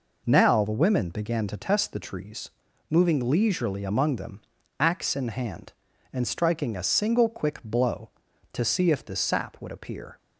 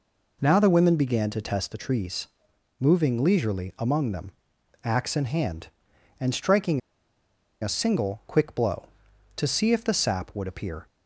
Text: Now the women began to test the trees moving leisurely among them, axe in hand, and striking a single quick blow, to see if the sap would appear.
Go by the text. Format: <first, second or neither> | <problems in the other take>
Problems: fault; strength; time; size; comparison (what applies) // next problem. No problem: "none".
first | pauses between "trees" and "moving"; noticeable; at 2.2 s; 0.52 s long; also in the first // pauses between "striking" and "a"; noticeable; at 6.8 s; 0.81 s long